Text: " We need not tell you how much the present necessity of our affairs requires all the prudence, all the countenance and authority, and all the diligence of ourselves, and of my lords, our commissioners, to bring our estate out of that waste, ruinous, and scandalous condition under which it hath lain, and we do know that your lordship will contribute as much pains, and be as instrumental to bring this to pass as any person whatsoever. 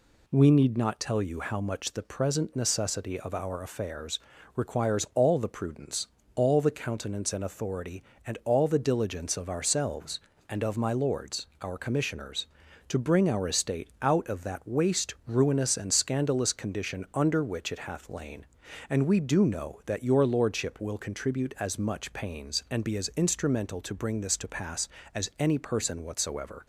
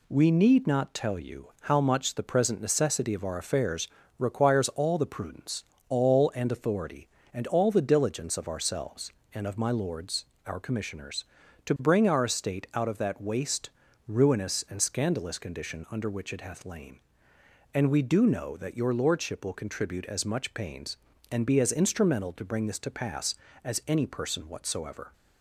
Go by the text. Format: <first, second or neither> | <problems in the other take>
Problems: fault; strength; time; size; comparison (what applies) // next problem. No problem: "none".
first | pauses between "affairs" and "requires"; slight; at 3.8 s; 0.32 s long; also in the first // skips "the countenance"; at 6.3 s